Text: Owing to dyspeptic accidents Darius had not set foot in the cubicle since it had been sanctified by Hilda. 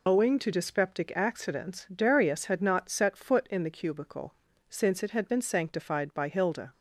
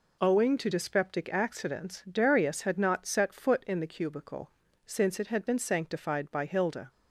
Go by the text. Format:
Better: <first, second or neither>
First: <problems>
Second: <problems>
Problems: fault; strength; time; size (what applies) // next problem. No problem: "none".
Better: second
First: loses the start of "Owing"; at 0.0 s; 50 ms // pauses between "cubicle" and "since"; slight; at 4.3 s; 0.36 s long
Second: pauses between "cubicle" and "since"; slight; at 4.4 s; 0.36 s long